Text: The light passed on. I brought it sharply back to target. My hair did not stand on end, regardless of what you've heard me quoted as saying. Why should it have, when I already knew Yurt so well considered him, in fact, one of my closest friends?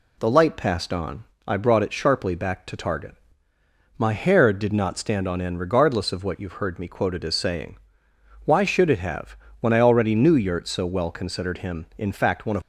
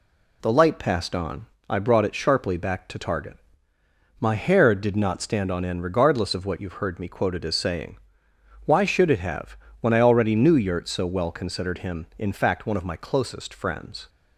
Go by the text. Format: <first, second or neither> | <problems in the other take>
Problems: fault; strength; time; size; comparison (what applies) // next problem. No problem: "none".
second | stops before "my closest friends"; at 12.6 s